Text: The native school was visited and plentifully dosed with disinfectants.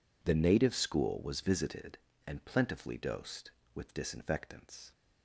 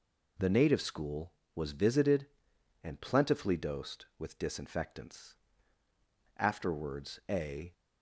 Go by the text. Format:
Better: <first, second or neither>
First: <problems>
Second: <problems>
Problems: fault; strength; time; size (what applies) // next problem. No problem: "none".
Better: first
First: none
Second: goes on to say "Afterwards a"; from 6.3 s on; 1.3 s long